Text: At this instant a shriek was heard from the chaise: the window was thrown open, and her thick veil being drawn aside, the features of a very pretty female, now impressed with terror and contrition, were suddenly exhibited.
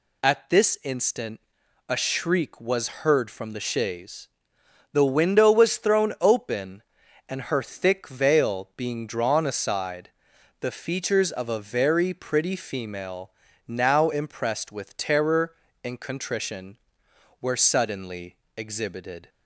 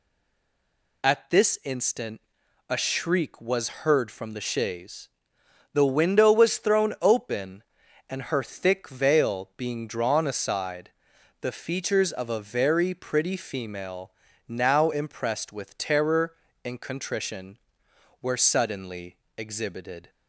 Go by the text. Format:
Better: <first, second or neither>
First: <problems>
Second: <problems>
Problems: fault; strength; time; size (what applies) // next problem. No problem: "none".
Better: first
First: pauses between "instant" and "a"; noticeable; at 1.3 s; 0.48 s long // pauses between "suddenly" and "exhibited"; slight; at 18.3 s; 0.22 s long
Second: stays silent before the first word; until 1.0 s; 1.0 s long // pauses between "instant" and "a"; noticeable; at 2.1 s; 0.48 s long // pauses between "suddenly" and "exhibited"; slight; at 19.1 s; 0.22 s long